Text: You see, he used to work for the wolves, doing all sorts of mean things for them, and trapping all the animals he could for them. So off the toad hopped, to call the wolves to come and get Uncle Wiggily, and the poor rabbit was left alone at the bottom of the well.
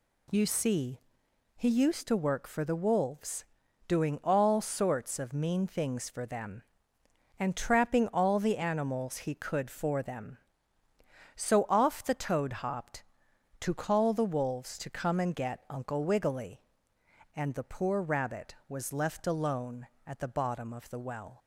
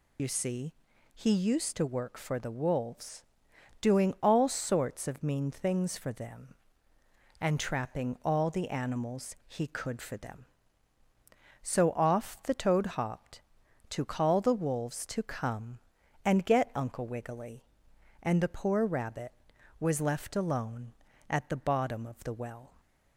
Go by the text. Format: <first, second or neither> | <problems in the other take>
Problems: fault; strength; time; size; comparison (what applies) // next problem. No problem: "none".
first | loses the start of "You"; at 0.1 s; 65 ms